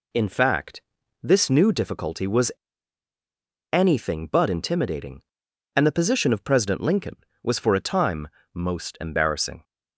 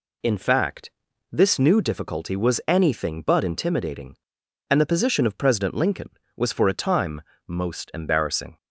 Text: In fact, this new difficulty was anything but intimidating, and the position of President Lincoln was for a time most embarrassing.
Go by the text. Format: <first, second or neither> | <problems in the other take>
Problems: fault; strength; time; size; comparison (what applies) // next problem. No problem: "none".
second | pauses between "was" and "anything"; at 2.5 s; 1.2 s long // pauses between "time" and "most"; slight; at 8.2 s; 0.26 s long; slight in the second